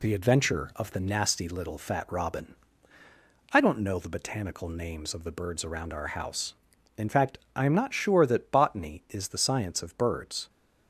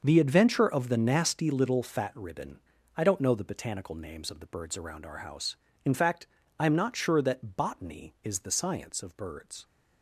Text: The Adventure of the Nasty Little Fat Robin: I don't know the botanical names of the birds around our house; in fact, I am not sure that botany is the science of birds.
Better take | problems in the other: first | starts louder than the rest; until 1.0 s; 6.5 dB // says "Ribbon" for "Robin"; at 2.1 s

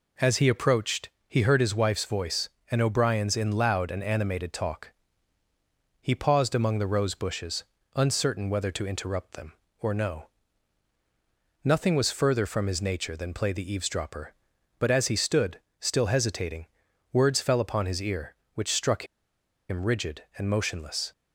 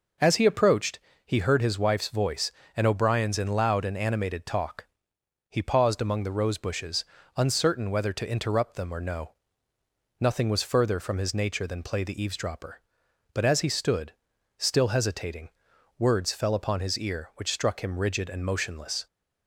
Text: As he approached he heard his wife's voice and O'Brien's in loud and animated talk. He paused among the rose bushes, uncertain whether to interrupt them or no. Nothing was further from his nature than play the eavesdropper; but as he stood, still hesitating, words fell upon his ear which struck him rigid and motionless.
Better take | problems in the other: second | pauses between "approached" and "he"; slight; at 1.0 s; 0.20 s long; slight in the second // pauses between "struck" and "him"; noticeable; at 19.0 s; 0.63 s long

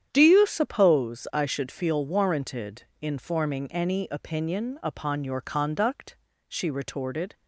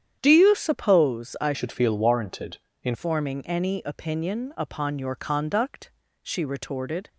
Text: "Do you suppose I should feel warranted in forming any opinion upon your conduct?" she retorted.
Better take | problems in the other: first | starts louder than the rest; strong; until 1.2 s; 9 dB; strong in the first // changes voice from "should" to "in"; from 1.5 to 2.9 s; 1.4 s long

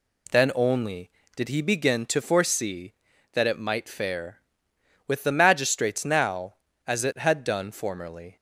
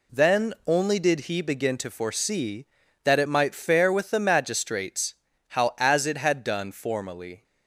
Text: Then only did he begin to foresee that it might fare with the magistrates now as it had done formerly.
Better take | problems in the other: first | says "how" for "now"; at 5.4 s

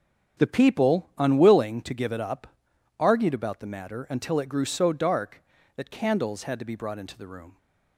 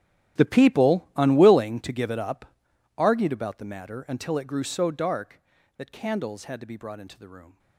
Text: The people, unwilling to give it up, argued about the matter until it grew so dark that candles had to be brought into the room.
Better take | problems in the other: first | gets quieter; strong; throughout; 18.5 dB // starts louder than the rest; strong; until 1.4 s; 11 dB; also in the first

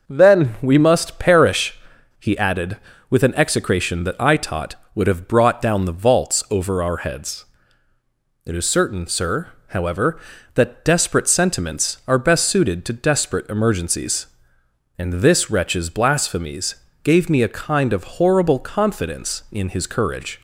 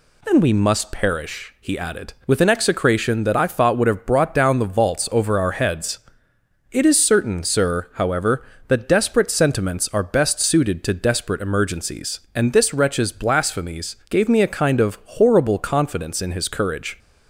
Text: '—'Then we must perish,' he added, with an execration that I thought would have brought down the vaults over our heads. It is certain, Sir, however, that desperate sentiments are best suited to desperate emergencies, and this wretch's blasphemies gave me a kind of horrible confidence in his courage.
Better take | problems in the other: second | says "taught" for "thought"; at 4.3 s // pauses between "blasphemies" and "gave"; slight; at 16.7 s; 0.30 s long

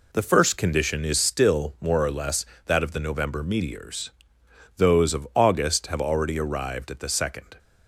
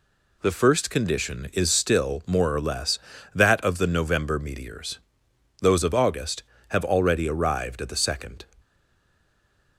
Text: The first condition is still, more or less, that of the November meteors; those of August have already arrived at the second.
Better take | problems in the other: first | stays silent after the last word; noticeable; from 8.5 s on; 1.2 s long

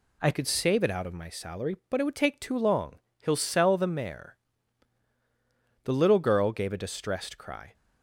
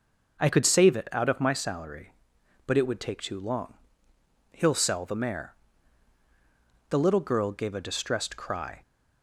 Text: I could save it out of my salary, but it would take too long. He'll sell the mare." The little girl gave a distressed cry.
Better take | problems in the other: second | changes voice at "could"; from 0.3 s on; 7.4 s long

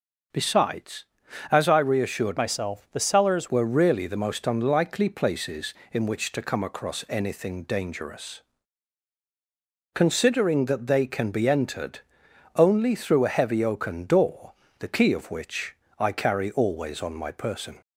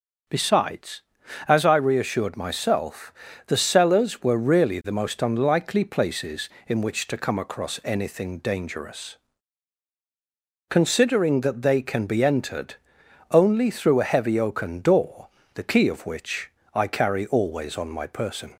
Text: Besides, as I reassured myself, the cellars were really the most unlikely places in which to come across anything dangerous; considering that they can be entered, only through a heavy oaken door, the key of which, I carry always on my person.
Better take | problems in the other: second | starts louder than the rest; until 1.7 s; 6.5 dB; also in the second // changes voice from "myself" to "cellars"; from 2.3 to 3.4 s; 1.1 s long

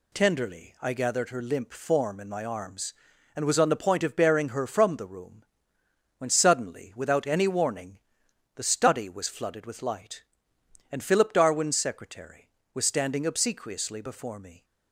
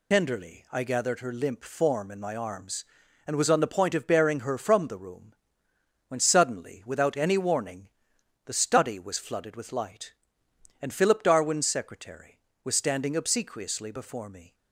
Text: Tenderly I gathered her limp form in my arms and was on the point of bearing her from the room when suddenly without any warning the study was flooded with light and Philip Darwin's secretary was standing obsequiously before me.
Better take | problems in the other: first | loses the start of "Tenderly"; at 0.1 s; 75 ms // pauses between "room" and "when"; noticeable; at 5.3 s; 0.76 s long; noticeable in the first // pauses between "warning" and "the"; noticeable; at 7.8 s; 0.56 s long; noticeable in the first

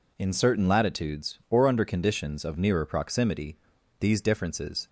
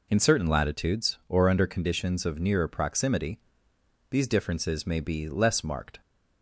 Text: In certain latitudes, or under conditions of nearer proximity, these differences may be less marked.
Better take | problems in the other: second | stops before "may be less marked"; at 4.8 s

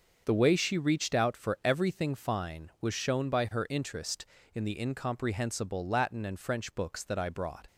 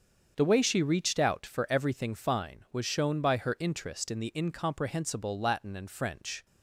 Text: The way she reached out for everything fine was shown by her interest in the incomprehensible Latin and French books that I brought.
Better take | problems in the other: first | starts louder than the rest; until 1.3 s; 7 dB; also in the first // stops before "books that I brought"; at 6.4 s

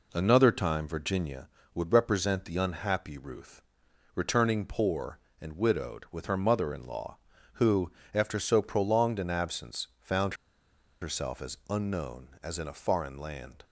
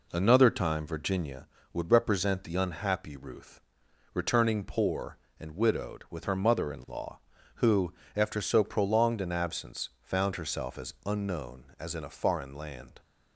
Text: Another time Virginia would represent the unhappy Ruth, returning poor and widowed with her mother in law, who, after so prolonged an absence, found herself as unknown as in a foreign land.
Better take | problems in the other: second | pauses between "found" and "herself"; noticeable; at 10.3 s; 0.67 s long

